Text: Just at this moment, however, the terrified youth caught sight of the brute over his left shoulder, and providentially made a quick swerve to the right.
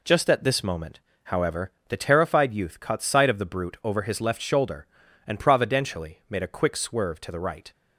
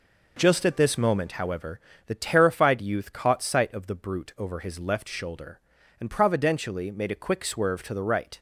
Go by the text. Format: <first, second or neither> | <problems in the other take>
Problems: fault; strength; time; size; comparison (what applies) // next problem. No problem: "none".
neither | none